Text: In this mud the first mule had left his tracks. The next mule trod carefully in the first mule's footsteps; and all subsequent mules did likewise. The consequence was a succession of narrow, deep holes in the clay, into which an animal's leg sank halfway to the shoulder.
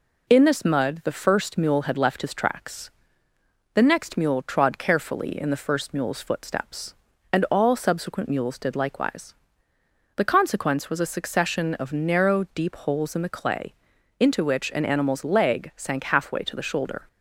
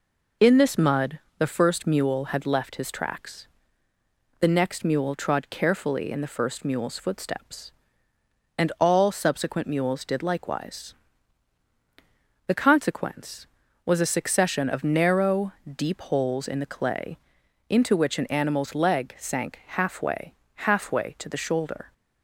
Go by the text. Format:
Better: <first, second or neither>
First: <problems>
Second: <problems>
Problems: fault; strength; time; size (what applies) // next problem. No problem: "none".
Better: first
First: none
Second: pauses between "mud" and "the"; slight; at 1.1 s; 0.20 s long // says "halfway" twice; at 20.5 s